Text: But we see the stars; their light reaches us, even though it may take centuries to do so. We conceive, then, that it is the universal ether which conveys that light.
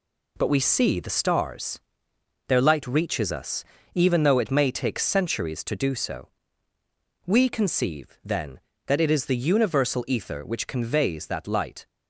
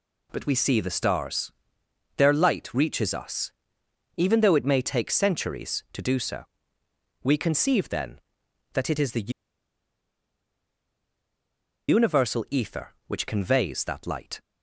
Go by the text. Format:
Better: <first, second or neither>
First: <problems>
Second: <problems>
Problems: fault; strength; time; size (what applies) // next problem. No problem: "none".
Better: first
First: none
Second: pauses between "the" and "universal"; strong; at 9.3 s; 2.5 s long